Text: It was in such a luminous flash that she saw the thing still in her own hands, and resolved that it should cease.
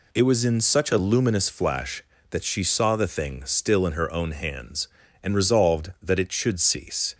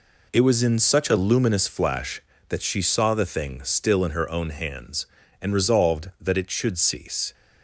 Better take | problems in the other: first | gets quieter; strong; throughout; 8.5 dB

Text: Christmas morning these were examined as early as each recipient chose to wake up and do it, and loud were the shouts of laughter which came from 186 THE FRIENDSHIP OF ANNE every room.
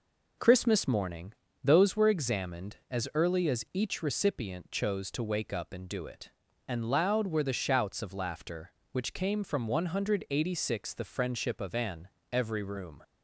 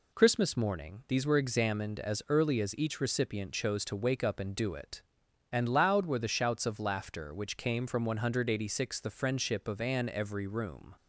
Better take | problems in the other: second | says "those" for "these"; at 1.6 s // pauses between "ANNE" and "every"; slight; at 12.0 s; 0.24 s long

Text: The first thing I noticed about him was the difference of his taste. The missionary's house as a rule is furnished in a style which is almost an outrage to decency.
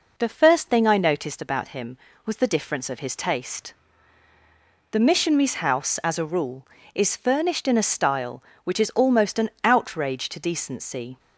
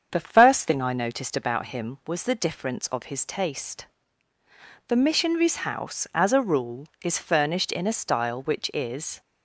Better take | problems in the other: first | starts louder than the rest; strong; until 1.1 s; 7 dB // stops before "almost an outrage to decency"; at 9.2 s

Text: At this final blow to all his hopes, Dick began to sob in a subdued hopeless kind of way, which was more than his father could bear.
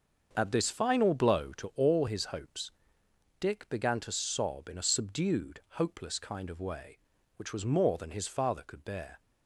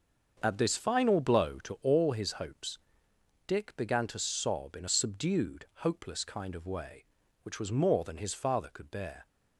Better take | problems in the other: neither | starts louder than the rest; the same in both

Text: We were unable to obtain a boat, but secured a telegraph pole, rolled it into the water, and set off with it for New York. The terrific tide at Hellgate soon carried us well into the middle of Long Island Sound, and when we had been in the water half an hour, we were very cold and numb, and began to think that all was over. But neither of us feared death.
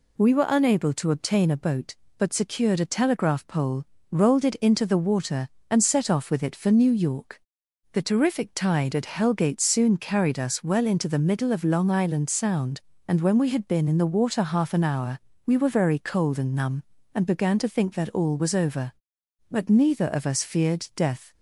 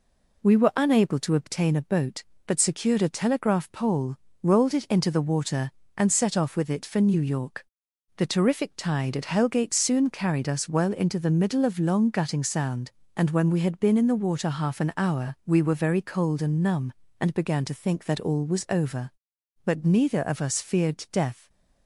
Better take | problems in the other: first | says "Gutting" for "Island"; at 12.0 s

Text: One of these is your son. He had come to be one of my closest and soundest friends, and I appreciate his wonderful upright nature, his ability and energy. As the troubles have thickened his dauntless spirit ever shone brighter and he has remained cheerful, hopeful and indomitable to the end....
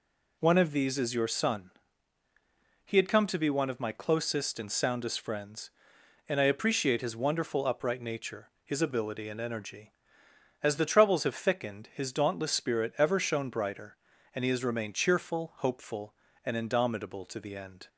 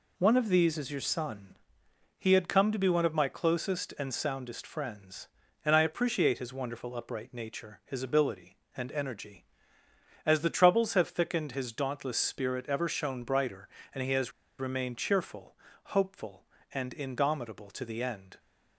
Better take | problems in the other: first | pauses between "has" and "remained"; slight; at 14.3 s; 0.27 s long

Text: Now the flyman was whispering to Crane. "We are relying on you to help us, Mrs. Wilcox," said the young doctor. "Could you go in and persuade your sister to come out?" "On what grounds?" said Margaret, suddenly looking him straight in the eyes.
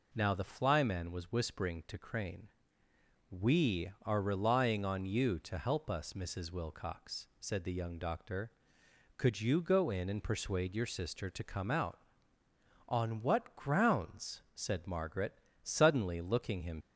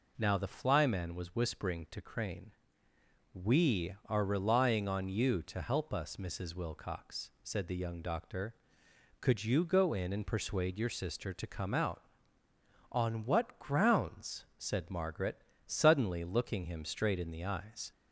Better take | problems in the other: second | stops before "straight in the eyes"; at 16.8 s

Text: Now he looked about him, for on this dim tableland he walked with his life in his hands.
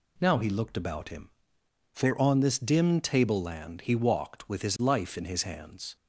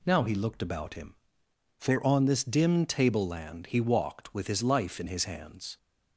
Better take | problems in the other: neither | none

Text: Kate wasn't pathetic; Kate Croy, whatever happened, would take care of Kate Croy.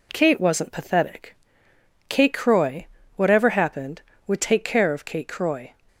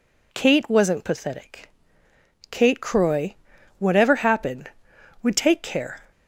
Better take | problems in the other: first | stops before "of Kate Croy"; at 6.1 s

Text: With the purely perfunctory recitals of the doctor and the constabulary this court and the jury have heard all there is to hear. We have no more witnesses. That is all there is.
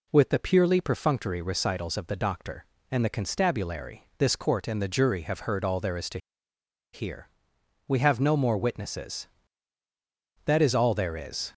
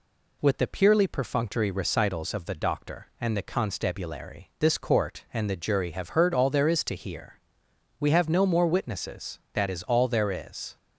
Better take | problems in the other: second | pauses between "to" and "hear"; noticeable; at 6.1 s; 0.75 s long

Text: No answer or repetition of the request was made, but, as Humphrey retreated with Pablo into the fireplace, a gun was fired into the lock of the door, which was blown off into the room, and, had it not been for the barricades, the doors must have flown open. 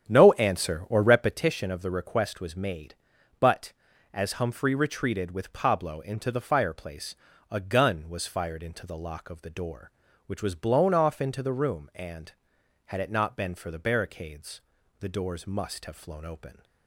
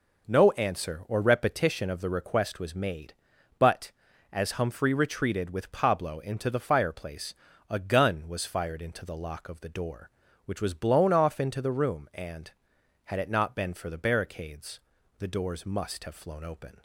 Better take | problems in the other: second | starts louder than the rest; strong; until 1.4 s; 9 dB

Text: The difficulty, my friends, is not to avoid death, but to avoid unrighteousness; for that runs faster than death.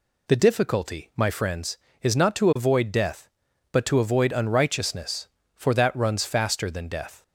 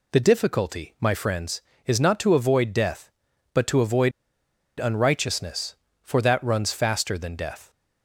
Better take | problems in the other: first | pauses between "avoid" and "unrighteousness"; noticeable; at 4.1 s; 0.68 s long

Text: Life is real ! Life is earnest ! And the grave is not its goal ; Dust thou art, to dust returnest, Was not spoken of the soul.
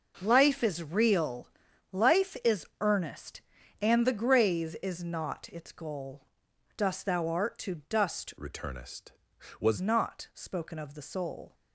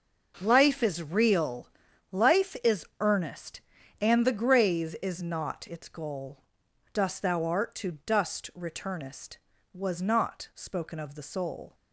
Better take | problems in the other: second | pauses between "is" and "earnest"; slight; at 2.6 s; 0.16 s long; slight in the second // changes voice from "returnest" to "Was"; from 8.3 to 9.7 s; 1.4 s long

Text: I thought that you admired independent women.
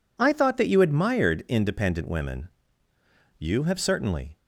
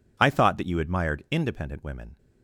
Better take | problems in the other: second | goes on to say "You have certainly"; noticeable; from 3.3 s on; 1.0 s long

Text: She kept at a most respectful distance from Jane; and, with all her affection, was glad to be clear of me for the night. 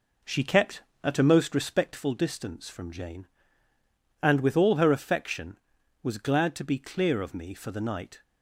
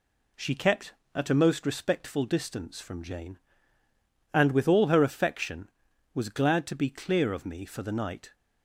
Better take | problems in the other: second | starts louder than the rest; noticeable; until 2.0 s; 4.5 dB

